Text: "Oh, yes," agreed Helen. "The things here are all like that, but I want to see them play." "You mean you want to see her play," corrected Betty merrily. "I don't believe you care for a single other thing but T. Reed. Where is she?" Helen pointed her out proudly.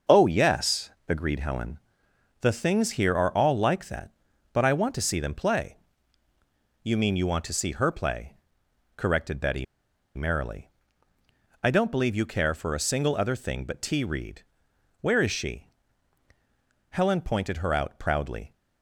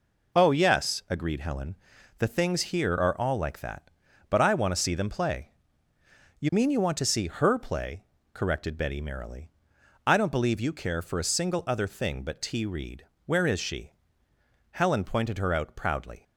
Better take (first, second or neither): second